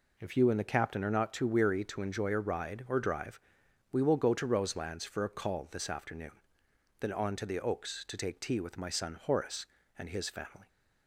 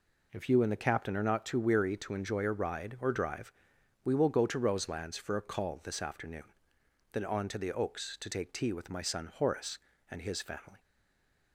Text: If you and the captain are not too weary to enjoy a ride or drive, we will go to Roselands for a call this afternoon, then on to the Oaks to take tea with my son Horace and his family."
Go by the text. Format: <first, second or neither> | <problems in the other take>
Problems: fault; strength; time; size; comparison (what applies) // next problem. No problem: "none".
first | stays silent after the last word; slight; from 10.7 s on; 0.8 s long